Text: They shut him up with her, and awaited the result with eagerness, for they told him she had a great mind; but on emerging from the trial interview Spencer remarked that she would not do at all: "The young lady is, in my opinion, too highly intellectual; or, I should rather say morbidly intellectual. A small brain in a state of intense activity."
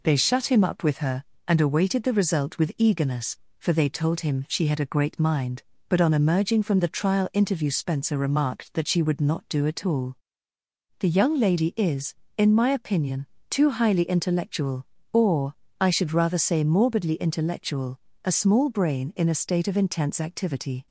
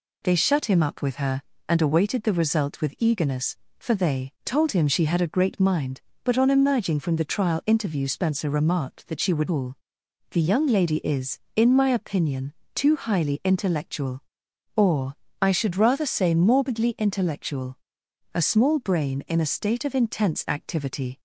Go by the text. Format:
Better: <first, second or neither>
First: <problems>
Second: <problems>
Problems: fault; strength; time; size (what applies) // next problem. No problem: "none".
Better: first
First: none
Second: skips "not do at"; at 9.4 s